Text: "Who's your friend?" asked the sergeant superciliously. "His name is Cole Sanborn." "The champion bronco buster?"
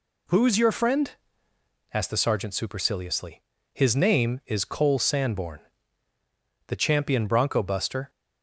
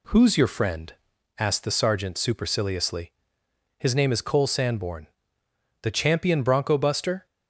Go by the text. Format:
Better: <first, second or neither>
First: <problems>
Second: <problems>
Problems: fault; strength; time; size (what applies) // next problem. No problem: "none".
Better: neither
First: none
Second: none